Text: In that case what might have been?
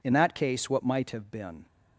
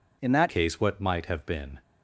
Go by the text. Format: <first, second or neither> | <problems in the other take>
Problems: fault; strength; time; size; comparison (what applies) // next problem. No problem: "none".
first | changes voice at "case"; from 0.4 s on; 1.4 s long